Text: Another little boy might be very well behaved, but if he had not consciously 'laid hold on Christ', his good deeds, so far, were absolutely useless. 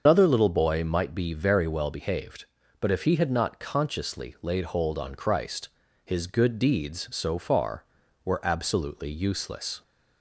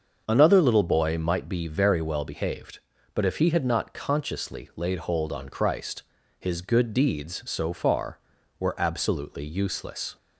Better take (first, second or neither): second